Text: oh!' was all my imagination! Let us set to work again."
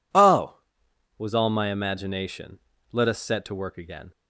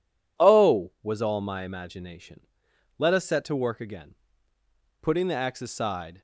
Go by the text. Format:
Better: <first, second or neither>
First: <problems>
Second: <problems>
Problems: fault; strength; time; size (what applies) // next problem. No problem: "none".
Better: first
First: none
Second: goes on to say "Putting the axe aside"; noticeable; from 5.0 s on; 1.2 s long